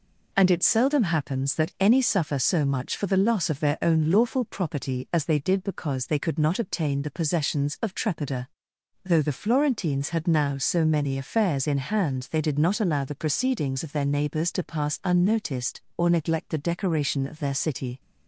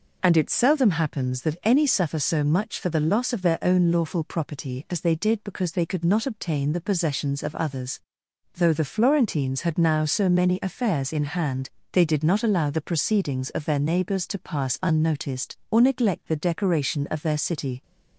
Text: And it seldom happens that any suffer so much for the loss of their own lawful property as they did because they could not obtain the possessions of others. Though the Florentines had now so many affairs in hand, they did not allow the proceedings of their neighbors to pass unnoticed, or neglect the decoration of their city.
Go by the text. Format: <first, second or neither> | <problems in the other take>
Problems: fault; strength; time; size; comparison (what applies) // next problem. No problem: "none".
second | says "trepida" for "others"; at 7.9 s